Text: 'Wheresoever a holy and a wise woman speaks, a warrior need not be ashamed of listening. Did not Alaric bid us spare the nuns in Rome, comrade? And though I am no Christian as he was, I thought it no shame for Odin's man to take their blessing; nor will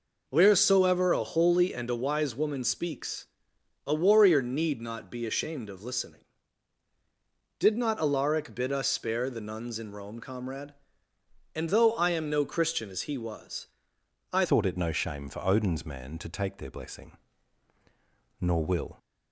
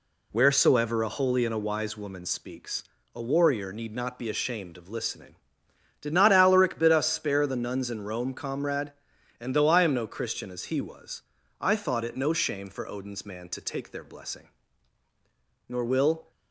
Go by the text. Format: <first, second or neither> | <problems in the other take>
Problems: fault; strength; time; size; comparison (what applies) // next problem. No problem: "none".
second | changes voice at "thought"; from 14.4 s on; 4.5 s long